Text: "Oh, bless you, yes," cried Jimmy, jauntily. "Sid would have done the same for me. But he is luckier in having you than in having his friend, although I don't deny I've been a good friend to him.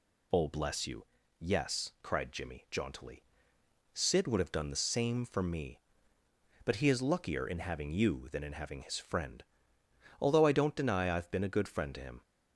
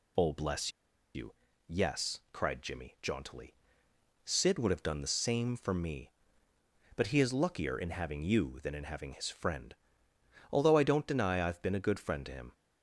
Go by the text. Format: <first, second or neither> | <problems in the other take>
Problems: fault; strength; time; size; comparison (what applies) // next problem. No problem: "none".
first | pauses between "bless" and "you"; at 0.7 s; 0.45 s long